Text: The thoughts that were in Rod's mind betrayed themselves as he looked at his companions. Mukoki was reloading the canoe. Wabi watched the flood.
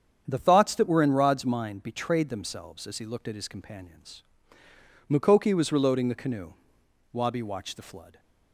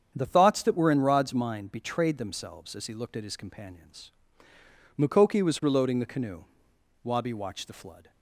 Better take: neither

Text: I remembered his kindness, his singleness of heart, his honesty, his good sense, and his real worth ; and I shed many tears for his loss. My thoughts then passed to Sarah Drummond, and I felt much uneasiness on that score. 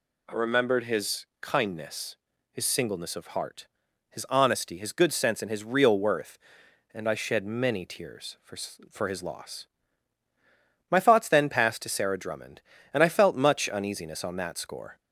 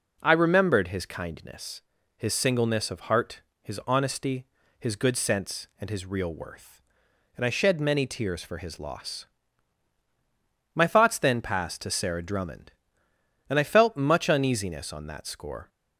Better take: second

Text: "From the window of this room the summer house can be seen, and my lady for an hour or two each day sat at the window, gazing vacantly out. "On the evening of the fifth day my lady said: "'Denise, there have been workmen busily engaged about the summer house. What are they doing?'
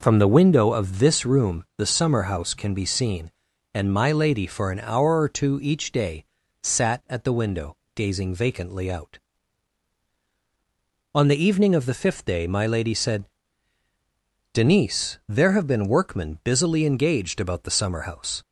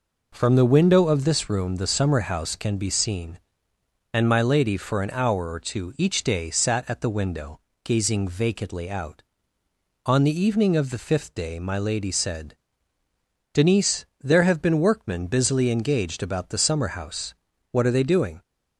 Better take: second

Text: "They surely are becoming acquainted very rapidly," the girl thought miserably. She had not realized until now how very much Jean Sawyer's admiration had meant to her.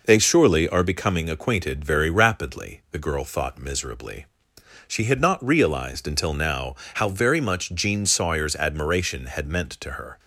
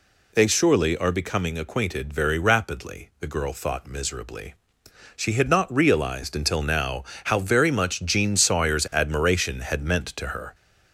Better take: first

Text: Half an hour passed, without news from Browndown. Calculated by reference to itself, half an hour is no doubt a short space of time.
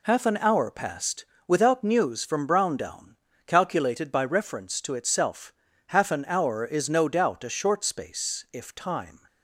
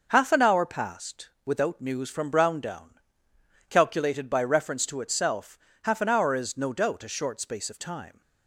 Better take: second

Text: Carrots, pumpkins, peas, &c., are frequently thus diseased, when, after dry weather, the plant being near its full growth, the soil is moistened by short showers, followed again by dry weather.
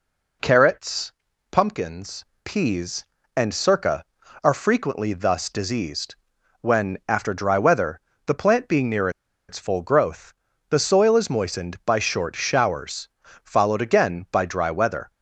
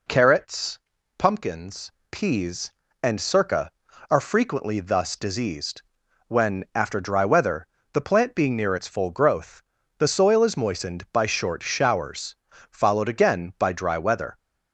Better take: second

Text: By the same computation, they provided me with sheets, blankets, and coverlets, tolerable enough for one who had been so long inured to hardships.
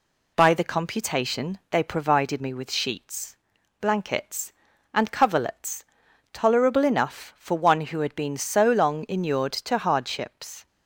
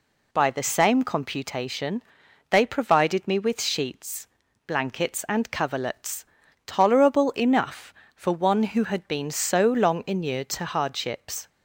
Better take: second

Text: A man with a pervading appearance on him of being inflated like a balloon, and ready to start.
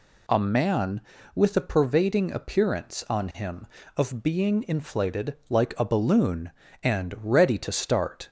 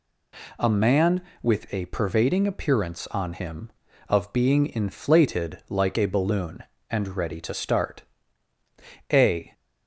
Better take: first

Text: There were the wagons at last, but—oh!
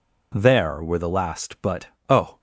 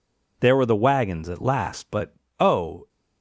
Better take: second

